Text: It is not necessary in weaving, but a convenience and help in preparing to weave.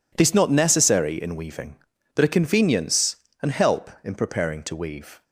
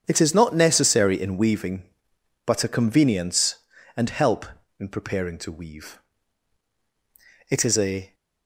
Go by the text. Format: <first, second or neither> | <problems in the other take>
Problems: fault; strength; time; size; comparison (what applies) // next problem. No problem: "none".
first | starts louder than the rest; strong; until 1.0 s; 8 dB // goes on to say "It is a"; noticeable; from 7.4 s on; 0.66 s long